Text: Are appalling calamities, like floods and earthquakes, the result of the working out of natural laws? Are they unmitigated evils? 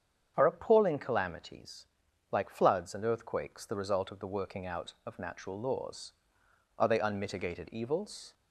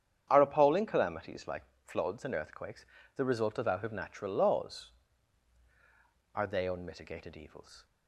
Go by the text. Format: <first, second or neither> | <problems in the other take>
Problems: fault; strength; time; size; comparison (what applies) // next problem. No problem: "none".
first | starts louder than the rest; strong; until 1.3 s; 9 dB; strong in the first // pauses between "like" and "floods"; slight; at 1.6 s; 0.22 s long // skips "the working"; at 3.6 s